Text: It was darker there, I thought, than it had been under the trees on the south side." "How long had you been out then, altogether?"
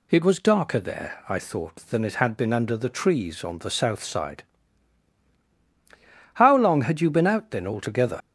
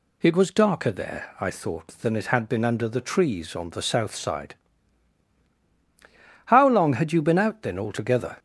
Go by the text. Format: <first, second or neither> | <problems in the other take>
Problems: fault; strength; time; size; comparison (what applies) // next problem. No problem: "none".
second | leaves "altogether" unfinished; at 8.2 s; 65 ms